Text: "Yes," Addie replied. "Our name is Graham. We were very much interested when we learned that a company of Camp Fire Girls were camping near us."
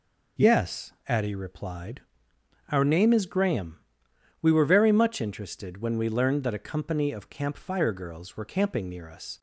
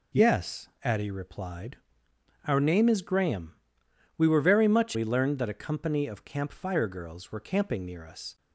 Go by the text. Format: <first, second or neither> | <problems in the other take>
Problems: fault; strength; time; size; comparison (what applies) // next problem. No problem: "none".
first | skips "interested when"; at 4.9 s